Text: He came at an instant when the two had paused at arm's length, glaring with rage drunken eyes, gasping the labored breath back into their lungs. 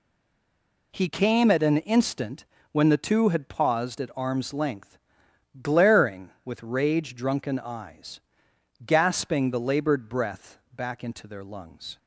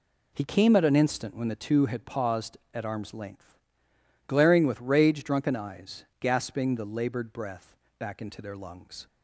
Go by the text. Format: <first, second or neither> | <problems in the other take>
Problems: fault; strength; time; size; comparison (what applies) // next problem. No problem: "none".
second | stays silent before the first word; slight; until 0.9 s; 0.9 s long // pauses between "instant" and "when"; slight; at 2.4 s; 0.28 s long // pauses between "breath" and "back"; slight; at 10.5 s; 0.16 s long; slight in the second